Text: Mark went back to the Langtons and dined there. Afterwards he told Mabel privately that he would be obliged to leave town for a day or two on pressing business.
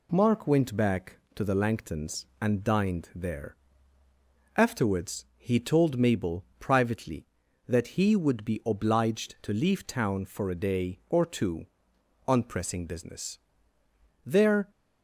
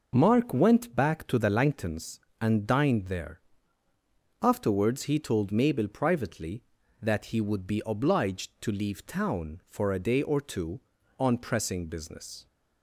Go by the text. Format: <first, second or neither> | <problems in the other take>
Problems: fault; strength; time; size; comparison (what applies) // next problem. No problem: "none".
second | goes on to say "There"; slight; from 14.2 s on; 0.44 s long